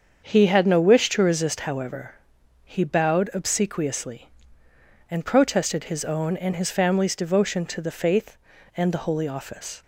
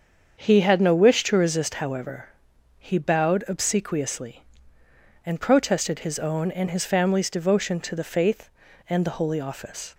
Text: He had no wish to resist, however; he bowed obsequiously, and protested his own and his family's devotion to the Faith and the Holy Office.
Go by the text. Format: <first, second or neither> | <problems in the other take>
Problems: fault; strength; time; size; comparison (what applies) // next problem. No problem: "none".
neither | starts louder than the rest; the same in both